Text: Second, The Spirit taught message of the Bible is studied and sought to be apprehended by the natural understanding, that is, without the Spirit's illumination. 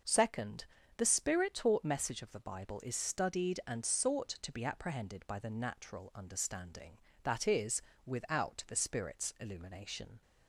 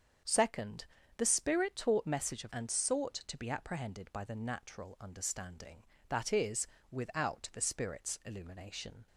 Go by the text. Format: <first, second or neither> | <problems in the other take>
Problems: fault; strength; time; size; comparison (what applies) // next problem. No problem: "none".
first | starts louder than the rest; strong; until 1.5 s; 7.5 dB; noticeable in the first // skips "the Bible is studied"; at 2.5 s